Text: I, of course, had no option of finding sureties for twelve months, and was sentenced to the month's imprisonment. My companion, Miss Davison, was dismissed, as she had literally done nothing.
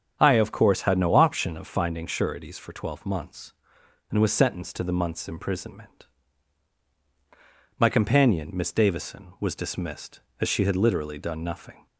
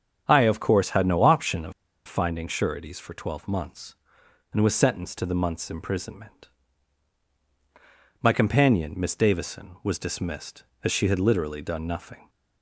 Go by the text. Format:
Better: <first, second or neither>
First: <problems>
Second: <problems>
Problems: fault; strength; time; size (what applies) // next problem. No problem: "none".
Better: first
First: starts louder than the rest; strong; until 1.2 s; 7.5 dB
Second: starts louder than the rest; strong; until 1.2 s; 8 dB // pauses between "of" and "finding"; slight; at 1.7 s; 0.34 s long